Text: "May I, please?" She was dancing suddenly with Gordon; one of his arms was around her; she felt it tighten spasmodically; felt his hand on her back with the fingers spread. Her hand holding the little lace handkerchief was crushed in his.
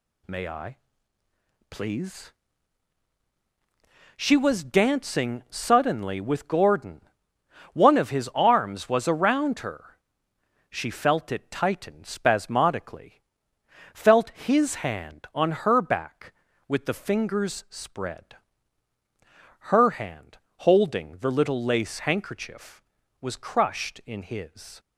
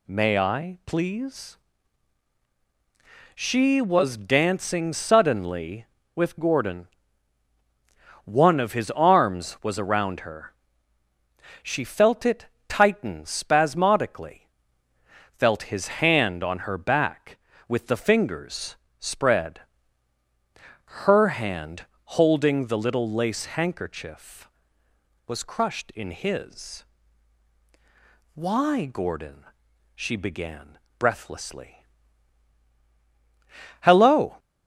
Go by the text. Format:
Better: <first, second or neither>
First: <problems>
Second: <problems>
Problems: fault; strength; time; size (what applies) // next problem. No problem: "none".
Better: first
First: pauses between "hand" and "holding"; slight; at 20.3 s; 0.22 s long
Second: pauses between "it" and "tighten"; slight; at 12.4 s; 0.22 s long // pauses between "fingers" and "spread"; slight; at 18.7 s; 0.22 s long // pauses between "hand" and "holding"; slight; at 21.8 s; 0.32 s long // goes on to say "Why Gordon she began breathlessly Hello"; strong; from 28.3 s on; 6.0 s long